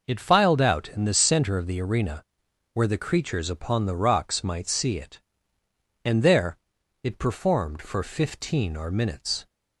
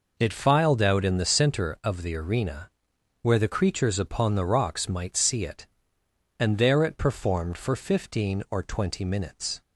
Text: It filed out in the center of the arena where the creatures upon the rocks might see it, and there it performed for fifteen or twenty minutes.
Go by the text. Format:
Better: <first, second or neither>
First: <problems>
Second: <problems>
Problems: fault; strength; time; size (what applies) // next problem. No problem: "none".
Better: second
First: pauses between "arena" and "where"; noticeable; at 2.2 s; 0.50 s long // pauses between "there" and "it"; at 6.5 s; 0.44 s long // skips "twenty"; at 8.9 s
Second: pauses between "arena" and "where"; noticeable; at 2.7 s; 0.50 s long